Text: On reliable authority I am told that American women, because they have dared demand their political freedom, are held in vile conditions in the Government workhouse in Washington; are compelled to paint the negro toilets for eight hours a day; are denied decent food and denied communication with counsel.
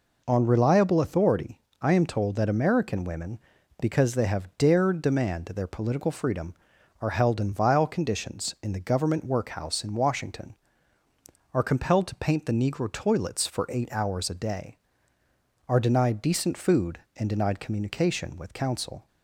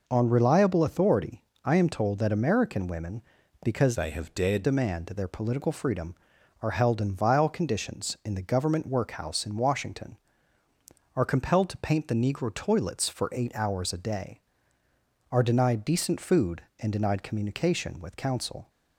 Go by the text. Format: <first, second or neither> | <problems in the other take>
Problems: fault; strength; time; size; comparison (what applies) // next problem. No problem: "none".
first | pauses between "authority" and "I"; slight; at 1.4 s; 0.22 s long; slight in the first // changes voice from "they" to "dared"; from 3.9 to 4.6 s; 0.7 s long